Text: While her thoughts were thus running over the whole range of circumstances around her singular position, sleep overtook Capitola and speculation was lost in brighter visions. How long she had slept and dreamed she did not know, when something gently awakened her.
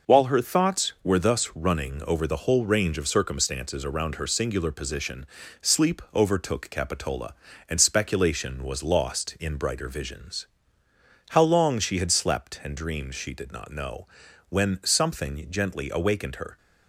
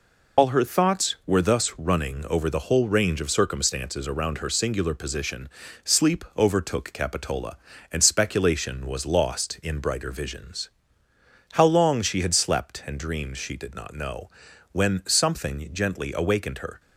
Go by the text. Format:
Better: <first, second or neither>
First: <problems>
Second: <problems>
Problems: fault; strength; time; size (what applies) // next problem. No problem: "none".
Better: first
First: none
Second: loses the start of "While"; at 0.3 s; 80 ms